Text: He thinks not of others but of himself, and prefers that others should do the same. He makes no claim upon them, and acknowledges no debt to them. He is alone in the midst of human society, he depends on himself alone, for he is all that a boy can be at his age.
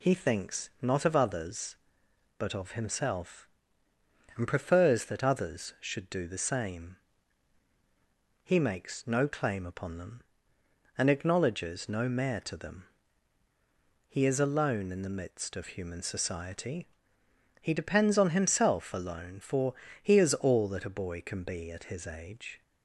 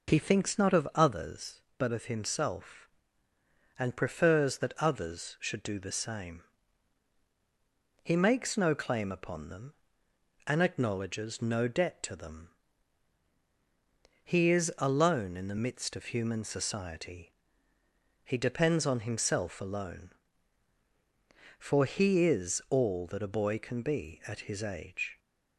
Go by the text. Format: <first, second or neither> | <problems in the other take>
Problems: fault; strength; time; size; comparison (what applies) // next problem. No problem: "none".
second | says "mayor" for "debt"; at 12.0 s // pauses between "for" and "he"; slight; at 19.7 s; 0.28 s long